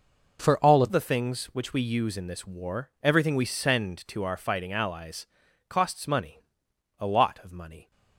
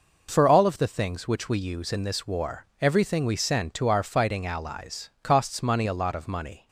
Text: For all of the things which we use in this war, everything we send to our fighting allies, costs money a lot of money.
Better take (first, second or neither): second